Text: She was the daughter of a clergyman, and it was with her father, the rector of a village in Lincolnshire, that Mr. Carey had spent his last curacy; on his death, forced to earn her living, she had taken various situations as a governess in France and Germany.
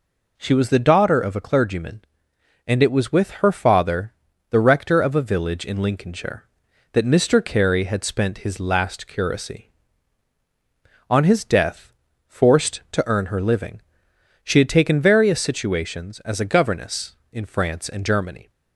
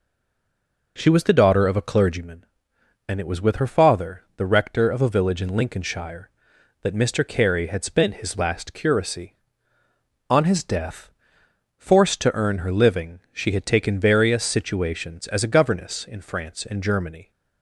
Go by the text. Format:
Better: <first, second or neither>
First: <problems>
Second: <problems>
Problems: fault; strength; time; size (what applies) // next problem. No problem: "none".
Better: first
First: none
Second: stays silent before the first word; slight; until 0.9 s; 0.9 s long